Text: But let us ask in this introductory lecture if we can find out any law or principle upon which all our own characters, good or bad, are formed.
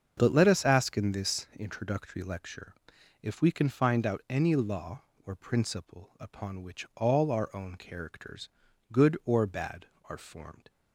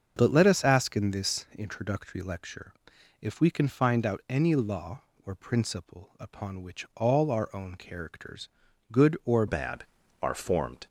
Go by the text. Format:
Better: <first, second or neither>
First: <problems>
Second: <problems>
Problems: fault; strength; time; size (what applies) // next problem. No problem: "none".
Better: first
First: starts louder than the rest; until 1.1 s; 7 dB // pauses between "lecture" and "if"; noticeable; at 2.7 s; 0.48 s long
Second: starts louder than the rest; until 1.1 s; 6.5 dB // pauses between "lecture" and "if"; noticeable; at 2.7 s; 0.48 s long // changes voice at "bad"; from 9.4 s on; 1.4 s long